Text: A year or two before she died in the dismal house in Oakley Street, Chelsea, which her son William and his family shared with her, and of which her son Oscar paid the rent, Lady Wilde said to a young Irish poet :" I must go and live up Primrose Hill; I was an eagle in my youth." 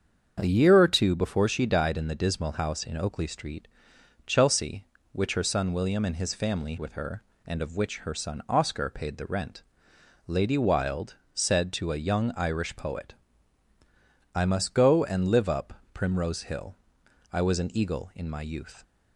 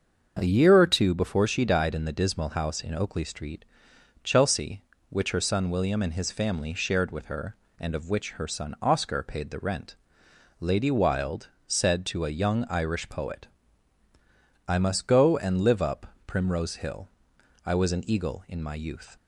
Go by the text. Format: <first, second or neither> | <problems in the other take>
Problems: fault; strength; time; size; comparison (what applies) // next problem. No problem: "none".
second | starts louder than the rest; until 1.4 s; 7 dB; also in the second // skips "shared"; at 6.7 s // pauses between "Wilde" and "said"; slight; at 11.1 s; 0.20 s long; slight in the second // pauses between "up" and "Primrose"; slight; at 15.7 s; 0.20 s long; slight in the second